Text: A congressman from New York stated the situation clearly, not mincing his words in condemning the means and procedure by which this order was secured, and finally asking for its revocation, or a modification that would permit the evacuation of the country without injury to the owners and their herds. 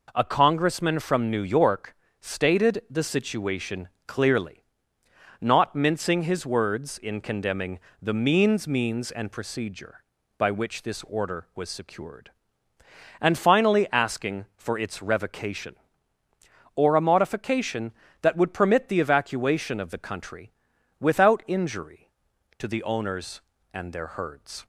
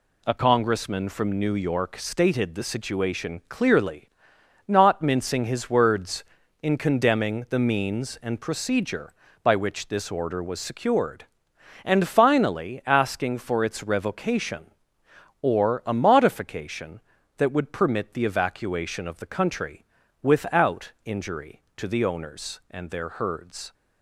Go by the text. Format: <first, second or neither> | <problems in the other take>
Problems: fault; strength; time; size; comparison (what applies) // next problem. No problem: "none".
second | pauses between "York" and "stated"; slight; at 1.9 s; 0.24 s long // pauses between "situation" and "clearly"; slight; at 3.8 s; 0.18 s long // pauses between "condemning" and "the"; slight; at 7.7 s; 0.22 s long // says "means" twice; at 8.6 s // pauses between "country" and "without"; noticeable; at 20.5 s; 0.48 s long; also in the second